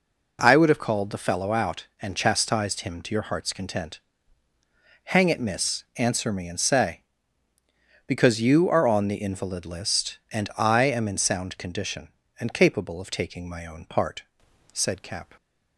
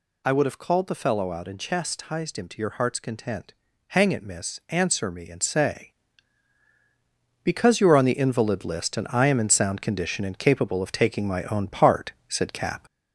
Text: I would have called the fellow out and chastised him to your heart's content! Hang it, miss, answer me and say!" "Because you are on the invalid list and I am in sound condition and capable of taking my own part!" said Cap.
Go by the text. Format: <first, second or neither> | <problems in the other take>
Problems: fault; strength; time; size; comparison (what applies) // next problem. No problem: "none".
first | gets louder; slight; throughout; 3.5 dB